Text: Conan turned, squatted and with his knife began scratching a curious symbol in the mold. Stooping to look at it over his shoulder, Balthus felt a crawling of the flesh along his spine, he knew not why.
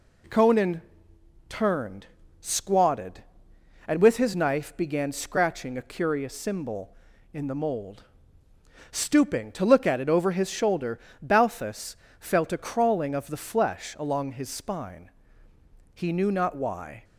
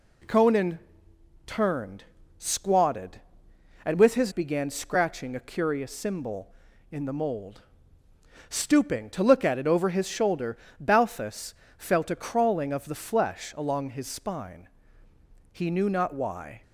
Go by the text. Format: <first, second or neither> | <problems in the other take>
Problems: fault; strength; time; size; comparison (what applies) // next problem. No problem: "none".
first | pauses between "Conan" and "turned"; noticeable; at 0.7 s; 0.68 s long; noticeable in the first // skips "knife"; at 4.3 s // pauses between "Balthus" and "felt"; slight; at 11.5 s; 0.20 s long; slight in the first